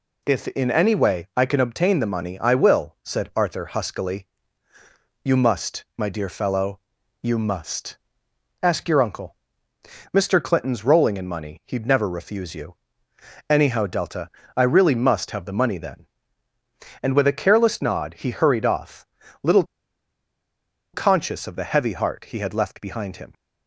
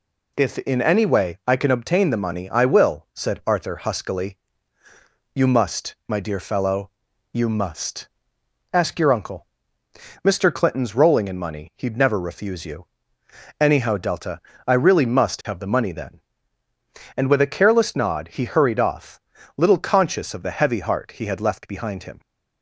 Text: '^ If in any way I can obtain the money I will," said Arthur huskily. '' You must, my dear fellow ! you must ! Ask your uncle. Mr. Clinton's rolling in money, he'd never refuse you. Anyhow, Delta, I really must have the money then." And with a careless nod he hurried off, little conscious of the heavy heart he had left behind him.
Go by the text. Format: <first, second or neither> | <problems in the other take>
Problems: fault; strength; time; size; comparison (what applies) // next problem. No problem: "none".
second | pauses between "little" and "conscious"; strong; at 19.6 s; 1.2 s long